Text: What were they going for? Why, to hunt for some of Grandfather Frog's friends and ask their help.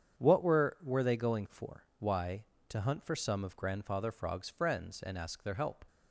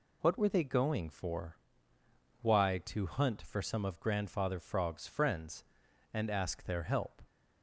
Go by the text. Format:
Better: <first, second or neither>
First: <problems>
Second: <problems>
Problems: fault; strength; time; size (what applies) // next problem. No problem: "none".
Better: second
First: starts louder than the rest; strong; until 1.2 s; 8 dB // says "were" twice; at 0.8 s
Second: none